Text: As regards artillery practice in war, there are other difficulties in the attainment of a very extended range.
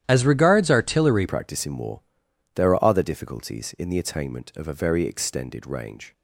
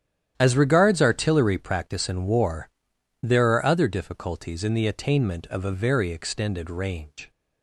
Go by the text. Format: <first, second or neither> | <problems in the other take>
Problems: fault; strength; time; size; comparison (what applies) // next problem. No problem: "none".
second | starts louder than the rest; strong; until 1.0 s; 11 dB; strong in the second // changes voice at "practice"; from 1.2 s on; 4.9 s long